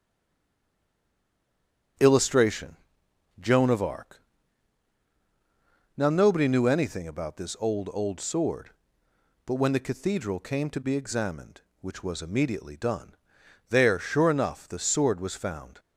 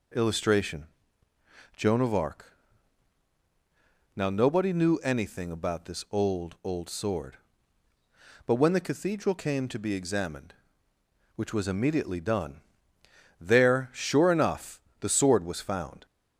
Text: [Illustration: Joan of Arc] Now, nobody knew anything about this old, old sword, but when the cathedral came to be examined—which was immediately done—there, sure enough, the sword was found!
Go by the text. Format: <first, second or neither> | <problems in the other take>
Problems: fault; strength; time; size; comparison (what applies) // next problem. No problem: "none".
second | stays silent before the first word; noticeable; until 1.9 s; 1.9 s long // starts louder than the rest; until 3.6 s; 6.5 dB // pauses between "Arc" and "Now"; strong; at 4.2 s; 1.7 s long; strong in the second